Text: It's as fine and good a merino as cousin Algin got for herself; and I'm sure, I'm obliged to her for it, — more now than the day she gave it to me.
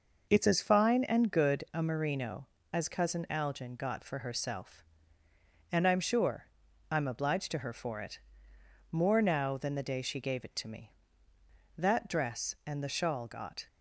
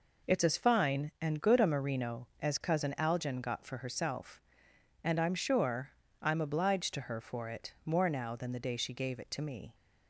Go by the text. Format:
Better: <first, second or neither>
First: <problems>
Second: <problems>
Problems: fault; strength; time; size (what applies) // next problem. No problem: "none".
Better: second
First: goes on to say "That dress and the shawl got"; strong; from 11.7 s on; 1.9 s long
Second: none